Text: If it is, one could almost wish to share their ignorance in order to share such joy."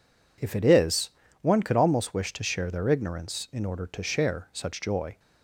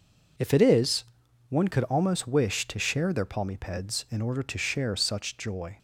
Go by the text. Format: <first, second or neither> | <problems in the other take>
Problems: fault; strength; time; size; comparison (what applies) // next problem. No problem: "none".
first | says "palmipeds" for "ignorance"; at 3.2 s